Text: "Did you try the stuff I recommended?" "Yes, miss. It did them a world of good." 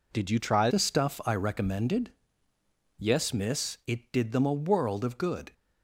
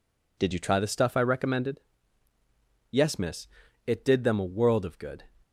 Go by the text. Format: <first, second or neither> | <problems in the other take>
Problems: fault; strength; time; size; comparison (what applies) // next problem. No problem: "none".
second | changes voice at "the"; from 0.6 s on; 4.9 s long